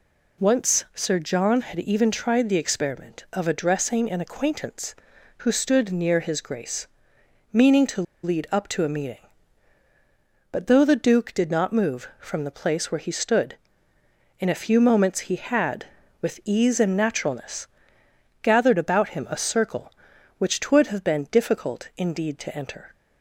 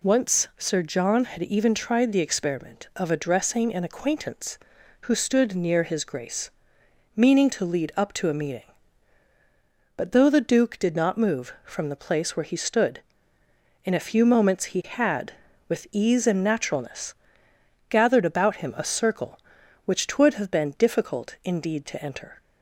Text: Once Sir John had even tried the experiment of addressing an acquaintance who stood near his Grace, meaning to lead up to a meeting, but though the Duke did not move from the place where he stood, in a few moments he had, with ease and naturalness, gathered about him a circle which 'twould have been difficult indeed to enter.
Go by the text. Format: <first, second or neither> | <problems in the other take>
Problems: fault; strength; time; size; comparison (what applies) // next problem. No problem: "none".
second | pauses between "to" and "lead"; slight; at 8.0 s; 0.21 s long